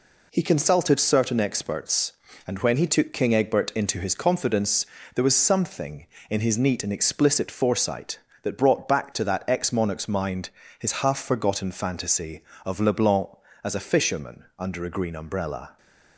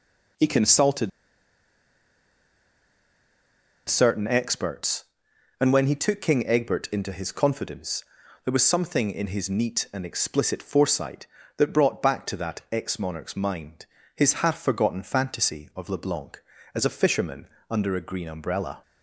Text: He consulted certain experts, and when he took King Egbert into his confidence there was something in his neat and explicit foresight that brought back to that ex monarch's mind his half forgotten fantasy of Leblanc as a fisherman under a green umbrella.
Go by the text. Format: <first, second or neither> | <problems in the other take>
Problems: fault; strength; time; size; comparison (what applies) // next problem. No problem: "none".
first | pauses between "consulted" and "certain"; strong; at 1.1 s; 2.7 s long // pauses between "confidence" and "there"; at 8.0 s; 0.40 s long; slight in the first // pauses between "mind" and "his"; slight; at 13.8 s; 0.32 s long; slight in the first // pauses between "fisherman" and "under"; slight; at 17.4 s; 0.22 s long